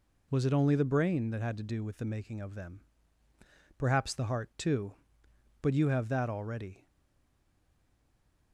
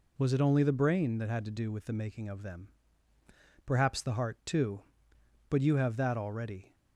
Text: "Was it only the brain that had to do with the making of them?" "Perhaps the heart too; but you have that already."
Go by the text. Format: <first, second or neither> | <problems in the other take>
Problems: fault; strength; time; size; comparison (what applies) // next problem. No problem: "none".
second | stays silent after the last word; noticeable; from 6.8 s on; 1.7 s long